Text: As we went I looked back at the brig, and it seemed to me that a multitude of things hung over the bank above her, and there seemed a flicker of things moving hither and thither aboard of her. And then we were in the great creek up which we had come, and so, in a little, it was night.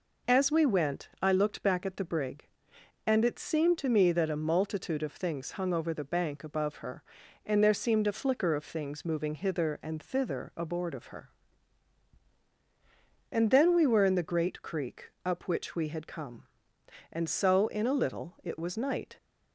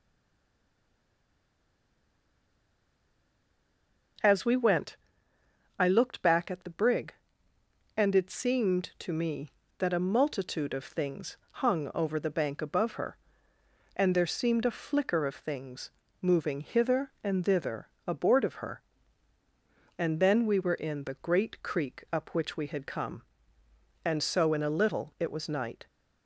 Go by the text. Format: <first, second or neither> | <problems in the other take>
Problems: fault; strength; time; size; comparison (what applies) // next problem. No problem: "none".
first | stays silent before the first word; strong; until 4.1 s; 4.1 s long // pauses between "went" and "I"; noticeable; at 4.9 s; 0.82 s long // pauses between "things" and "moving"; slight; at 15.9 s; 0.32 s long // pauses between "thither" and "aboard"; slight; at 17.8 s; 0.18 s long